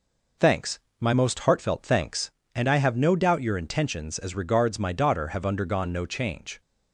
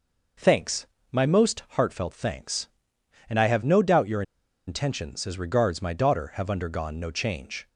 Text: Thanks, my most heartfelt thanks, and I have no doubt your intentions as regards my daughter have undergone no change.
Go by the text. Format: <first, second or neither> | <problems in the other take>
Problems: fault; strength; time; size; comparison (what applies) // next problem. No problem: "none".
first | pauses between "your" and "intentions"; at 4.2 s; 0.45 s long